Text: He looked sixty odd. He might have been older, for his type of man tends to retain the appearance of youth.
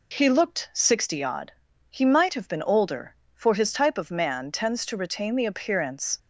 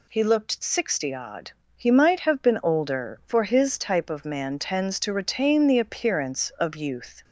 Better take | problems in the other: second | stops before "of youth"; at 6.1 s

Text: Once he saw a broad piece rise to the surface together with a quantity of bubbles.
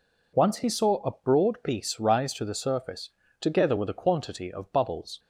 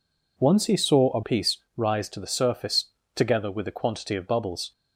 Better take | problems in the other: first | skips "broad"; at 1.2 s // pauses between "piece" and "rise"; slight; at 1.5 s; 0.18 s long // pauses between "surface" and "together"; slight; at 2.8 s; 0.30 s long; slight in the first

